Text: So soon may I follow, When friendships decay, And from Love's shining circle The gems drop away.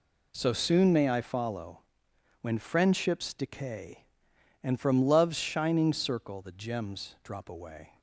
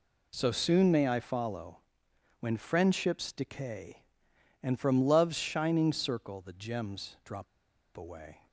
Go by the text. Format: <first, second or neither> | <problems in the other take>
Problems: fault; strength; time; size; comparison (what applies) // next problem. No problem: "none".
first | pauses between "drop" and "away"; noticeable; at 7.4 s; 0.49 s long